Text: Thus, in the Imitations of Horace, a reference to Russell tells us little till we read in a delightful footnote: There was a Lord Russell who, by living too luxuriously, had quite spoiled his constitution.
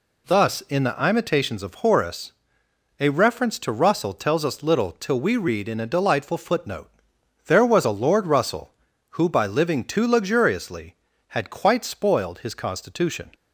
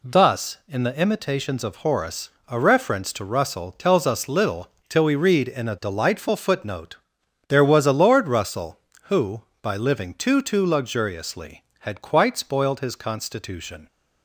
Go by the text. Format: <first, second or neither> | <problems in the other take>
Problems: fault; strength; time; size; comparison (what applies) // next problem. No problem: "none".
first | pauses between "little" and "till"; slight; at 4.6 s; 0.20 s long // says "too" twice; at 10.4 s